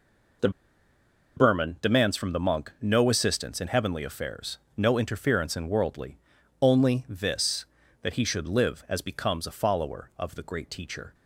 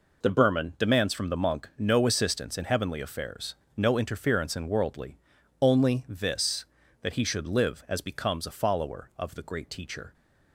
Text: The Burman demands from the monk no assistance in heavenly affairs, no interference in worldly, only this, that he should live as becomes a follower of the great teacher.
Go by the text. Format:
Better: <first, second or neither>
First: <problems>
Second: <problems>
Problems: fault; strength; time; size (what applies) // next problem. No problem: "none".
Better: second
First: pauses between "The" and "Burman"; noticeable; at 0.4 s; 0.87 s long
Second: none